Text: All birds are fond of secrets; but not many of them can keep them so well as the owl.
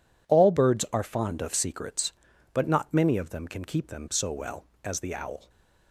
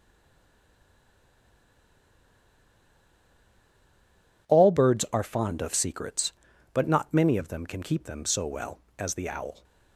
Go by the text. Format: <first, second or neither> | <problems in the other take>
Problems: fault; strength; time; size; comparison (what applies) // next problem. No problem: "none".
first | stays silent before the first word; strong; until 4.4 s; 4.4 s long